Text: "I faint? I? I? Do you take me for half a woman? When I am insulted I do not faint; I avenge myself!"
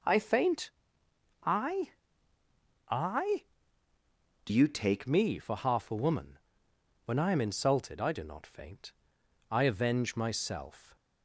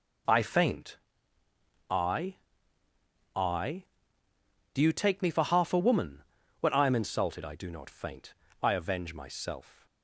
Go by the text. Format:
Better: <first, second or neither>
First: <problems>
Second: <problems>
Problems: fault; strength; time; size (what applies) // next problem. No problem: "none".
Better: second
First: changes voice from "you" to "take"; from 4.4 to 5.0 s; 0.6 s long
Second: none